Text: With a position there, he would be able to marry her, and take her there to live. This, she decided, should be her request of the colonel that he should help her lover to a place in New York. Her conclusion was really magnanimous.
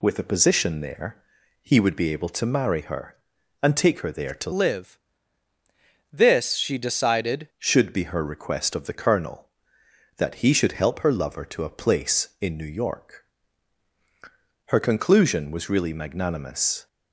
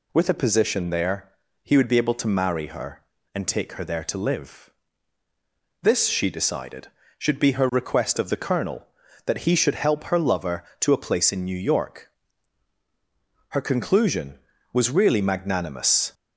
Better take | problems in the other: second | changes voice from "live" to "decided"; from 4.5 to 7.4 s; 2.9 s long

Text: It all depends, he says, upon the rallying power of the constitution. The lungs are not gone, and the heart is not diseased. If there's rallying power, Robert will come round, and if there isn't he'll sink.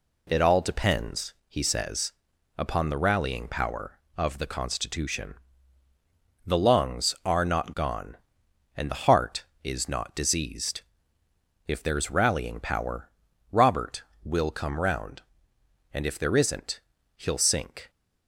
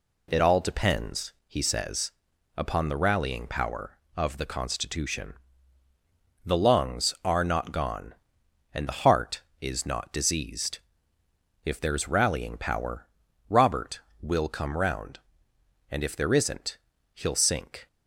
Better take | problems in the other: neither | pauses between "isn't" and "he'll"; slight; the same in both

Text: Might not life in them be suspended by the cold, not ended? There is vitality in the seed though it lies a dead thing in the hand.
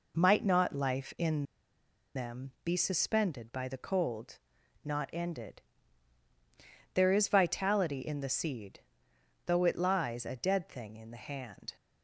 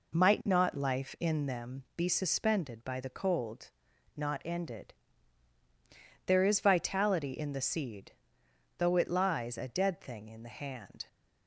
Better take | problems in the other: second | pauses between "in" and "them"; noticeable; at 1.4 s; 0.71 s long // pauses between "seed" and "though"; noticeable; at 8.8 s; 0.64 s long; noticeable in the second

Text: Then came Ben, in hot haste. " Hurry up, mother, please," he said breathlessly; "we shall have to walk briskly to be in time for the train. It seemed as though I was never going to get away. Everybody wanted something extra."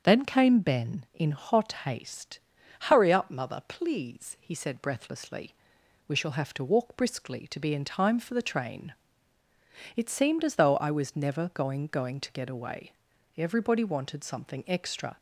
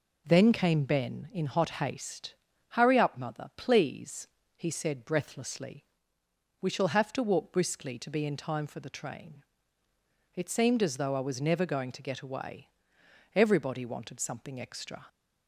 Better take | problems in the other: second | starts louder than the rest; until 1.0 s; 7 dB // says "going" twice; at 11.8 s

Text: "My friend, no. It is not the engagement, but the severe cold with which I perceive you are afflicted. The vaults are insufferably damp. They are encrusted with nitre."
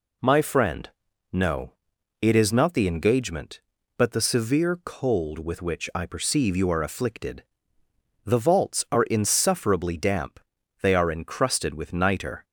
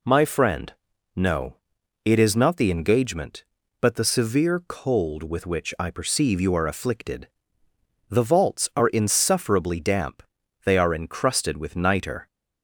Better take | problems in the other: neither | none

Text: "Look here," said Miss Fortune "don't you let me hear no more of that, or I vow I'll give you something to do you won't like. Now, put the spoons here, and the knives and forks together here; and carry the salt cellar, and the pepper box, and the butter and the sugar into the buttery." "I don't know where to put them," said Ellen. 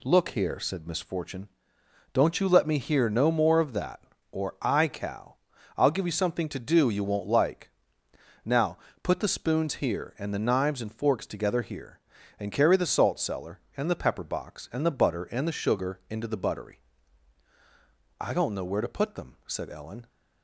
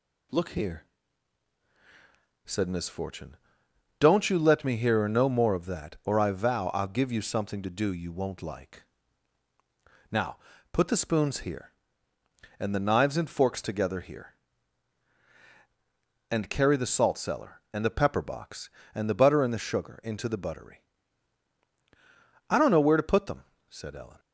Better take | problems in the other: second | pauses between "Fortune" and "don't"; noticeable; at 1.4 s; 0.64 s long; noticeable in the second // says "cow" for "vow"; at 4.8 s

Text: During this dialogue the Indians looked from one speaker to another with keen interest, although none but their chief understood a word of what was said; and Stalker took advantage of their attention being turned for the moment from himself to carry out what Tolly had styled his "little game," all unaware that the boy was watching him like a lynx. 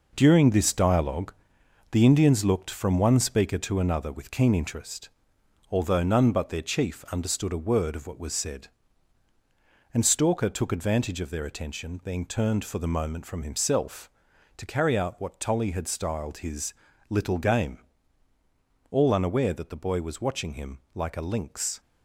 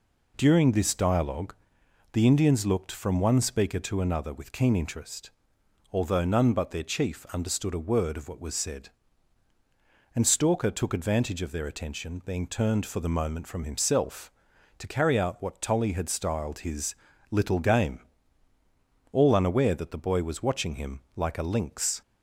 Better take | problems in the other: second | gets quieter; throughout; 7 dB // pauses between "dialogue" and "the"; noticeable; at 1.3 s; 0.56 s long; noticeable in the second // pauses between "his" and "little"; slight; at 16.7 s; 0.36 s long; slight in the second // pauses between "him" and "like"; slight; at 20.7 s; 0.16 s long; slight in the second

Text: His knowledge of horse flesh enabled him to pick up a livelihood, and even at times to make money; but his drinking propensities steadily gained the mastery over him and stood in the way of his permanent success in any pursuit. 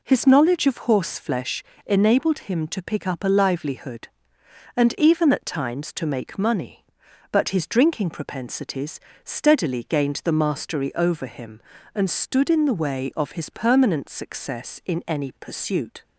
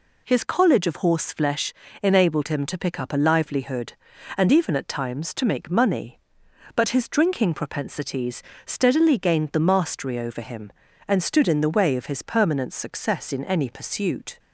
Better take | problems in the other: first | says "college" for "knowledge"; at 0.4 s // pauses between "flesh" and "enabled"; slight; at 1.7 s; 0.30 s long; slight in the first // pauses between "propensities" and "steadily"; slight; at 8.4 s; 0.22 s long; slight in the first

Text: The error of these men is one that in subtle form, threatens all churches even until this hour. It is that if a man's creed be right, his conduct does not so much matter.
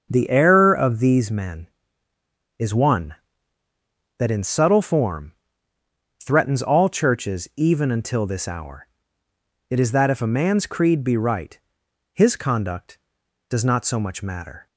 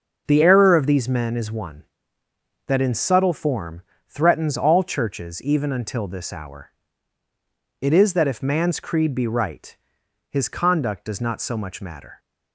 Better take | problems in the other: first | starts louder than the rest; until 1.2 s; 6.5 dB; also in the first // skips "a"; at 8.4 s

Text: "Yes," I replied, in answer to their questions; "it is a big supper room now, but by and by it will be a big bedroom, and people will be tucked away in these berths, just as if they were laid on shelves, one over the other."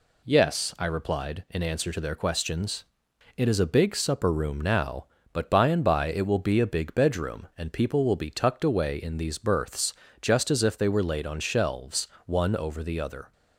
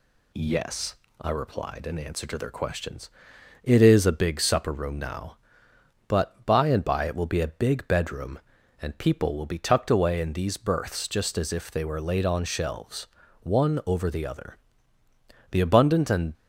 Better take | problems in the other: first | goes on to say "The abundant and"; noticeable; from 15.5 s on; 0.82 s long

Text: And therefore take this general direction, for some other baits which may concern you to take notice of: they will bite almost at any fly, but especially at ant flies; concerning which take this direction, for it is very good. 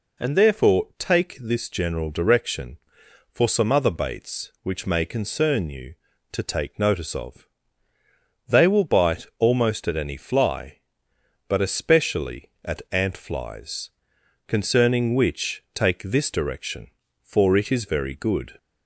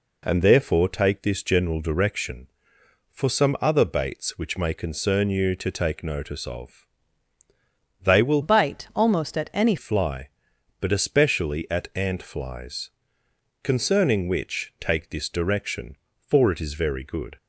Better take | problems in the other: first | changes voice from "bite" to "any"; from 8.4 to 9.7 s; 1.3 s long

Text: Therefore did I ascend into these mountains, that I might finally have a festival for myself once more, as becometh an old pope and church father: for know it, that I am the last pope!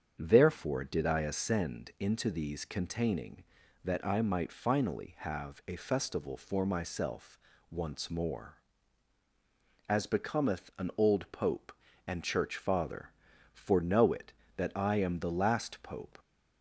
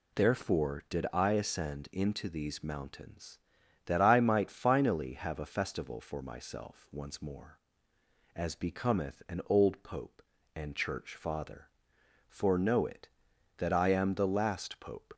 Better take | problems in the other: second | starts louder than the rest; strong; until 1.1 s; 7.5 dB // says "containing" for "mountains"; at 2.6 s // pauses between "myself" and "once"; slight; at 7.3 s; 0.32 s long

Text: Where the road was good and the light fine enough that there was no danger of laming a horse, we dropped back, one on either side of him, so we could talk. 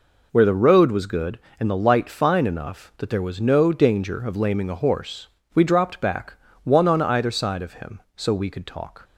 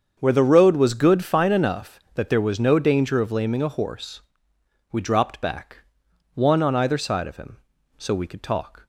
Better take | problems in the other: first | starts louder than the rest; until 1.2 s; 7 dB // skips "and the light"; at 1.2 s

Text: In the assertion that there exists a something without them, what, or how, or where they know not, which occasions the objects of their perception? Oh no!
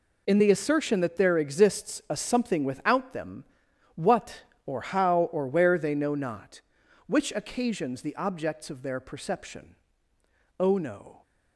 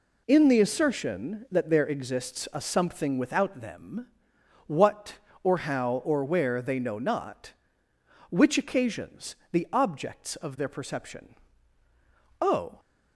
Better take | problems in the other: first | pauses between "occasions" and "the"; slight; at 9.3 s; 0.16 s long // stops before "no"; at 12.7 s

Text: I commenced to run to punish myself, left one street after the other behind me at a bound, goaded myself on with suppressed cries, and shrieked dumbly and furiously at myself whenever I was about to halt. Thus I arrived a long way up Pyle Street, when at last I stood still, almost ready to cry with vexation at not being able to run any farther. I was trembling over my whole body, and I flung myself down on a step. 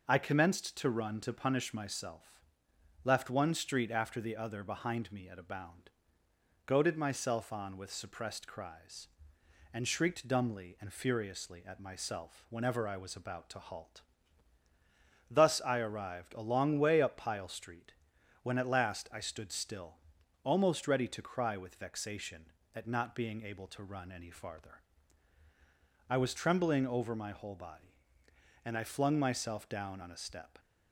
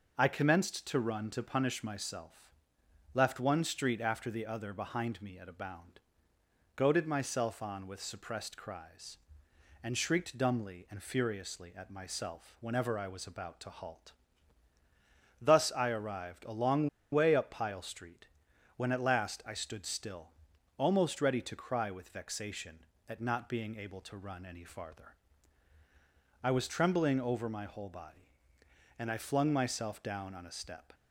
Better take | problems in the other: first | pauses between "long" and "way"; slight; at 16.8 s; 0.24 s long

